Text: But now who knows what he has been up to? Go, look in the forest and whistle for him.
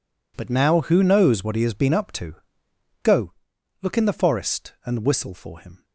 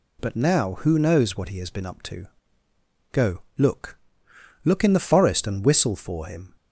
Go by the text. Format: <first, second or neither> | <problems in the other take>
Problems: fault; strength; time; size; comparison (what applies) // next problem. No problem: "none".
first | says "look" twice; at 4.6 s